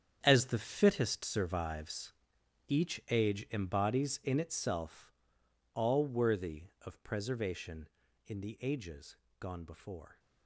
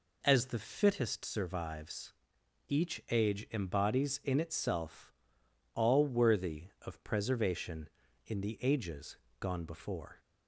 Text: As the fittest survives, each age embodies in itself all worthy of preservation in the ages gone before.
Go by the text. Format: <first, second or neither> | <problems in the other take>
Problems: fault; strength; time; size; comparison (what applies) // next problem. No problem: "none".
second | gets quieter; strong; throughout; 13 dB // pauses between "itself" and "all"; noticeable; at 5.1 s; 0.62 s long; noticeable in the second // pauses between "ages" and "gone"; slight; at 9.1 s; 0.22 s long; slight in the second